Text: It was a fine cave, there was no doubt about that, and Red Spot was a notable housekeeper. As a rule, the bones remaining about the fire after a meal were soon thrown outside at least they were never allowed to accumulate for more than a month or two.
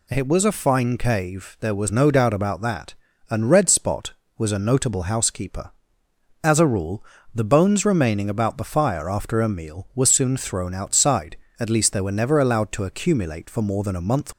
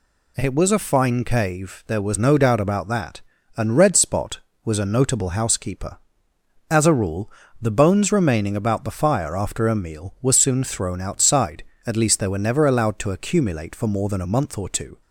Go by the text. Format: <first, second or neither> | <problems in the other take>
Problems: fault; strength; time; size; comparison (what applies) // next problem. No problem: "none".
second | stops before "or two"; at 14.3 s